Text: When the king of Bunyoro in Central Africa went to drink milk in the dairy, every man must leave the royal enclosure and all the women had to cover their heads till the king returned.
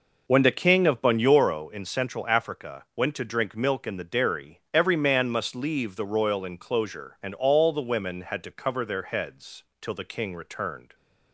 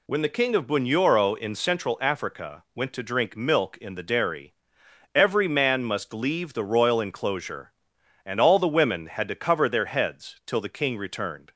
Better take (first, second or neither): second